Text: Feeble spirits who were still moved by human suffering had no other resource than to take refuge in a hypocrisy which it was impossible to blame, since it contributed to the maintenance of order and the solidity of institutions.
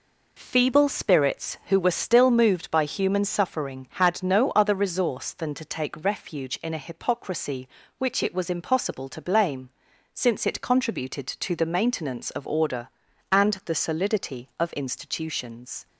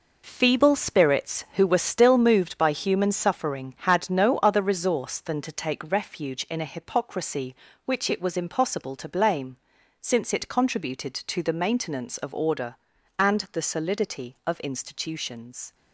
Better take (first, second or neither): first